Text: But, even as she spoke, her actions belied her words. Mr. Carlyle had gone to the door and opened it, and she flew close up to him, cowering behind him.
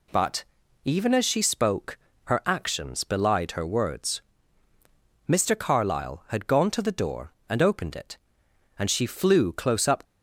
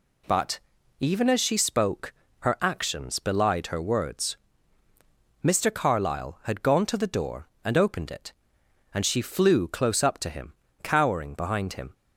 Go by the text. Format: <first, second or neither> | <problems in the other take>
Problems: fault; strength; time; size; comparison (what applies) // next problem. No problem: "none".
second | stops before "to him cowering behind him"; at 10.0 s